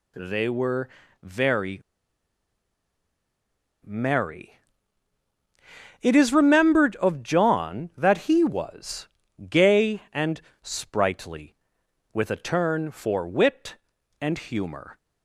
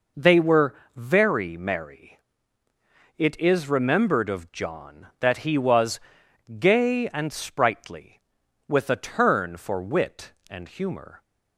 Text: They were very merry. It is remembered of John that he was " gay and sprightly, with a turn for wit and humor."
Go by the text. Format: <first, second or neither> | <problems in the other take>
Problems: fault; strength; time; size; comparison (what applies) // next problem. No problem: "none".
second | pauses between "were" and "very"; slight; at 0.8 s; 0.34 s long; slight in the second // pauses between "very" and "merry"; strong; at 1.8 s; 2.0 s long // pauses between "and" and "sprightly"; slight; at 10.4 s; 0.20 s long